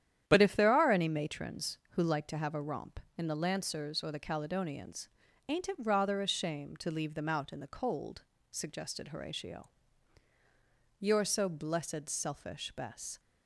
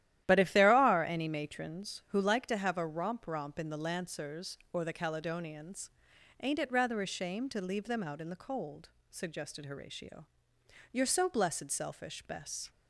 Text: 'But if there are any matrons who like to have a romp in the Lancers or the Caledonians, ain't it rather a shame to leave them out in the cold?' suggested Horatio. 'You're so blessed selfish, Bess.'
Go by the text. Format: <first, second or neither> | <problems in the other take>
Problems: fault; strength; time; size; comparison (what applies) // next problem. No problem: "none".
first | starts louder than the rest; strong; until 1.2 s; 12.5 dB; strong in the first // says "romp" twice; at 3.2 s